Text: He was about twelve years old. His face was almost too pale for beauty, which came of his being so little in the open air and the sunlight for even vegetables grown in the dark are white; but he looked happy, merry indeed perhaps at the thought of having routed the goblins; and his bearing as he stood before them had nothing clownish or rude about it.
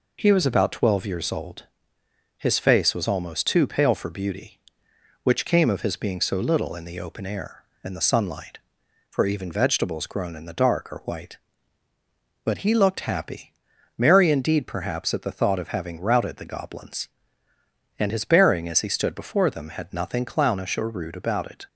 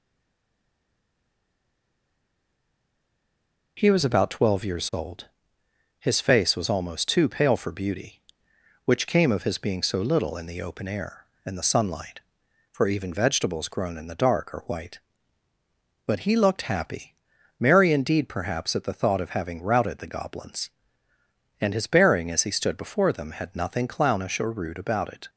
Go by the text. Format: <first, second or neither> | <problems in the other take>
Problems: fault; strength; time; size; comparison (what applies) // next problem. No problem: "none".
first | stays silent before the first word; strong; until 3.7 s; 3.7 s long